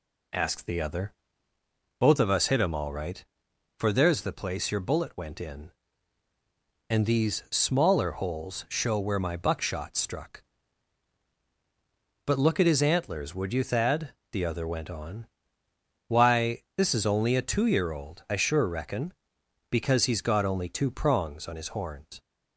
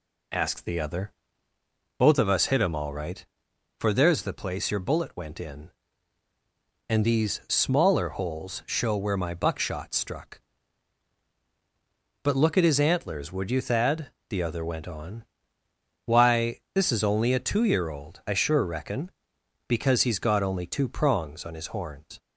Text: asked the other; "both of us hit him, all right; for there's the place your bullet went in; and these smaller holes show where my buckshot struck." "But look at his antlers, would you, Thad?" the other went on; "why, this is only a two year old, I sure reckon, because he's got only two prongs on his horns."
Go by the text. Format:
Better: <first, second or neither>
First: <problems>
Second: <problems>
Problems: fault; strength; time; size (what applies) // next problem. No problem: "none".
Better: neither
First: none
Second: none